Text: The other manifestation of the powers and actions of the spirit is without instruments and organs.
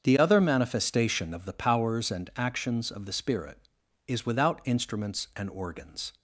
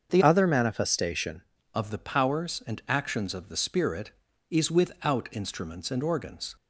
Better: first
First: starts louder than the rest; until 1.0 s; 7 dB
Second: starts louder than the rest; until 1.1 s; 7 dB // changes voice from "other" to "manifestation"; from 0.2 to 1.4 s; 1.2 s long

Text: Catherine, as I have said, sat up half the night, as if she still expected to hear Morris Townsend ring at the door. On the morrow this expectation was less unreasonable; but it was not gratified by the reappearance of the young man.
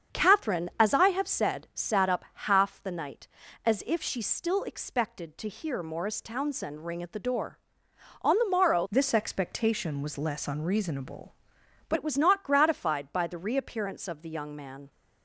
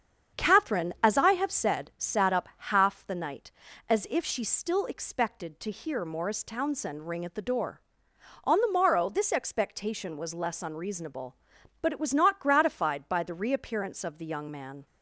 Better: second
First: starts louder than the rest; strong; until 1.2 s; 7.5 dB // changes voice from "this" to "but"; from 8.9 to 11.9 s; 3.0 s long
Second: starts louder than the rest; strong; until 1.4 s; 7.5 dB

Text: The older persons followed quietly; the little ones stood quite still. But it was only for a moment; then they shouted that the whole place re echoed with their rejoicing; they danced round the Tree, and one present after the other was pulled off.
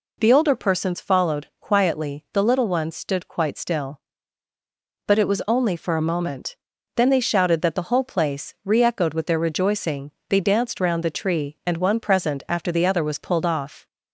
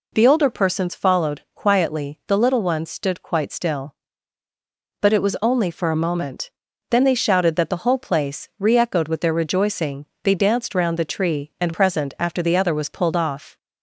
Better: first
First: none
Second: skips "one"; at 11.7 s

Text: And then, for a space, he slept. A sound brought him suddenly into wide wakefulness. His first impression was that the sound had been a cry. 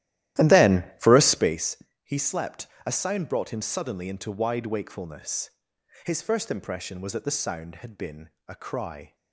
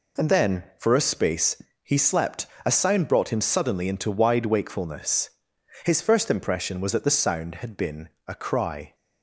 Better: second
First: starts louder than the rest; strong; until 1.6 s; 14 dB // pauses between "been" and "a"; slight; at 8.2 s; 0.18 s long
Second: pauses between "been" and "a"; slight; at 8.0 s; 0.18 s long

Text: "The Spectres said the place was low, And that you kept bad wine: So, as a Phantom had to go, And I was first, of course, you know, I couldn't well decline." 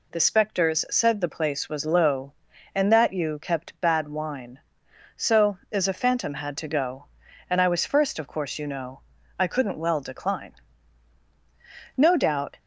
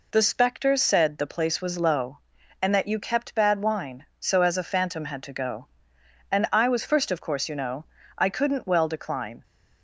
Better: second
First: goes on to say "No doubt"; noticeable; from 11.9 s on; 0.62 s long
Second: none

